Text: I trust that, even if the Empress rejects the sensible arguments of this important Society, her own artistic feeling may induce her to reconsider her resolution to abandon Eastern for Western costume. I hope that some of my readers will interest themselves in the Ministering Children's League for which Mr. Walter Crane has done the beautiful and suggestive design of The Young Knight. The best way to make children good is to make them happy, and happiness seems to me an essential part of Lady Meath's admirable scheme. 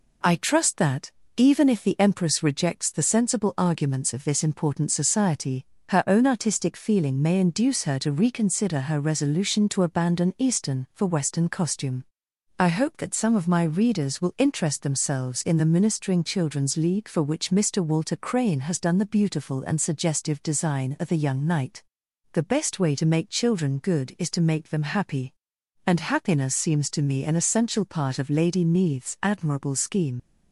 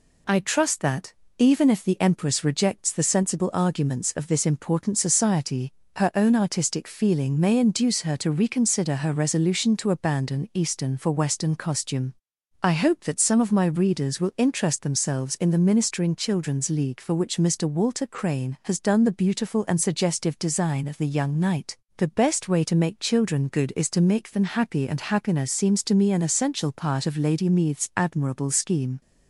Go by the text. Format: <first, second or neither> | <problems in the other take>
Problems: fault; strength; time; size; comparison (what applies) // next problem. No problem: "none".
second | leaves "scheme" unfinished; at 30.1 s; 60 ms